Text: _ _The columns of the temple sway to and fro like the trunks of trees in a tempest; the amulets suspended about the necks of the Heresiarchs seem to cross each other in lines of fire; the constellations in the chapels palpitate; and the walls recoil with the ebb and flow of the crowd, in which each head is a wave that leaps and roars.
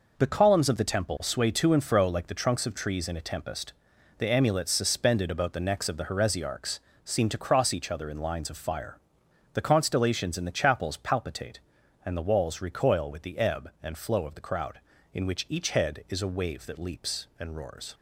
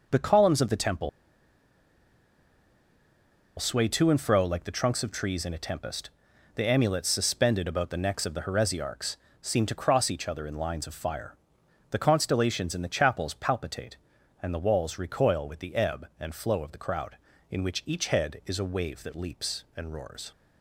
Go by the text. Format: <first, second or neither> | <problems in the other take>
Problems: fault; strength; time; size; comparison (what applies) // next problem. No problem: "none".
first | pauses between "temple" and "sway"; strong; at 1.0 s; 2.4 s long // pauses between "Heresiarchs" and "seem"; slight; at 9.1 s; 0.24 s long; slight in the first